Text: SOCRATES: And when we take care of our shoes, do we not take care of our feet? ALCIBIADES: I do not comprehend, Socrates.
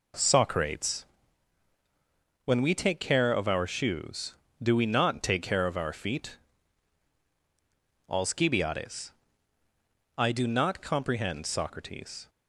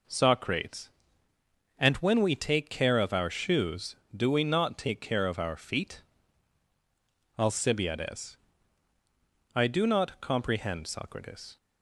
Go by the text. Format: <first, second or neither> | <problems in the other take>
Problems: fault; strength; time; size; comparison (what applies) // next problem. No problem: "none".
second | skips "And"; at 1.7 s